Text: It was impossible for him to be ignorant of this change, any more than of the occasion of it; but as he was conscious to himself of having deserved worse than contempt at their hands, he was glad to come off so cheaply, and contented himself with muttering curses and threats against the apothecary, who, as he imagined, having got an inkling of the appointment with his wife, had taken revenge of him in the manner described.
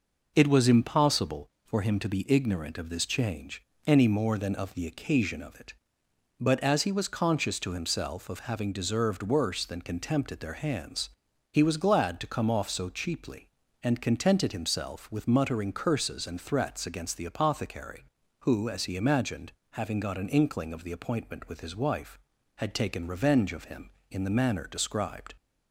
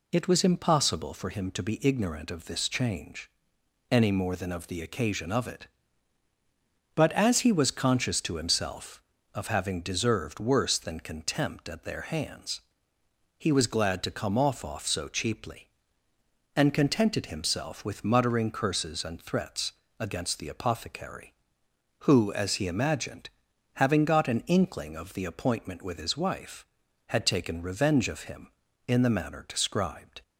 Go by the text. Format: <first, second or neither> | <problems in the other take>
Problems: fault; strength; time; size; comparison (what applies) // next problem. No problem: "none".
first | says "off" twice; at 14.6 s // pauses between "threats" and "against"; slight; at 19.7 s; 0.26 s long